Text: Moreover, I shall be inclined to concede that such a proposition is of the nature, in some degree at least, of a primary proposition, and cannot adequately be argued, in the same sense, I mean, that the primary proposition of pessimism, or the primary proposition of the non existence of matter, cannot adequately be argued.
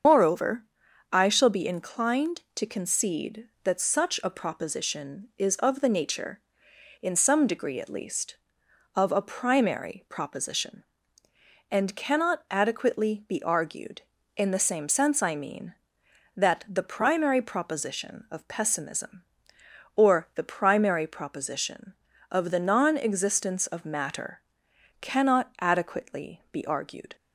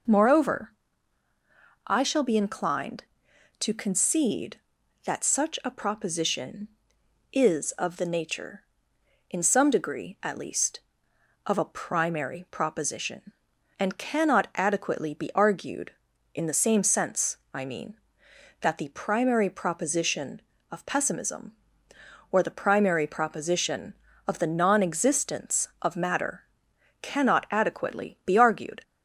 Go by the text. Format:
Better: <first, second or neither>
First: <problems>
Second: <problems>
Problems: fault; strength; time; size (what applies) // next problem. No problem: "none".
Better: second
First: loses the start of "Moreover"; at 0.0 s; 85 ms // starts louder than the rest; strong; until 1.5 s; 7 dB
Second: none